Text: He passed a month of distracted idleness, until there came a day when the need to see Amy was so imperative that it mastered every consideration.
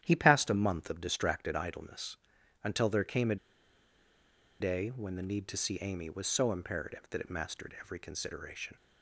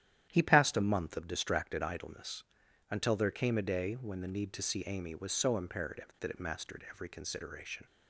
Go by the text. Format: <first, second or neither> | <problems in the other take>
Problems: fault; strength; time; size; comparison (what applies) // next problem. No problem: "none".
second | starts louder than the rest; strong; until 1.0 s; 11 dB; strong in the second // pauses between "a" and "day"; at 3.3 s; 1.2 s long